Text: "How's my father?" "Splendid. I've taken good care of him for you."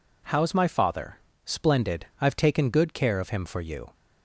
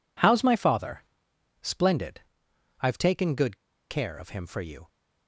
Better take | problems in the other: first | pauses between "good" and "care"; slight; at 3.5 s; 0.33 s long

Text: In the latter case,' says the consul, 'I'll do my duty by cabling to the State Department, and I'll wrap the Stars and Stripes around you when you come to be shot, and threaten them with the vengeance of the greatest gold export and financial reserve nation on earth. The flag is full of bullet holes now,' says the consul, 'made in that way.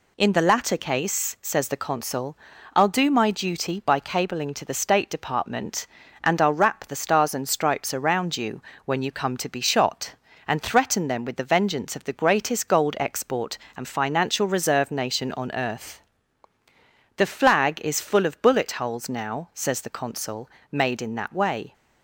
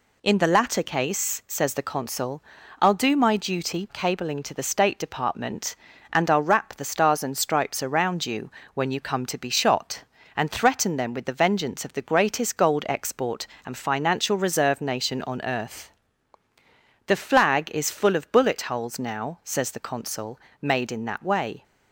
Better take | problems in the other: first | skips "by"; at 3.8 s // pauses between "you" and "when"; slight; at 8.5 s; 0.22 s long; slight in the first

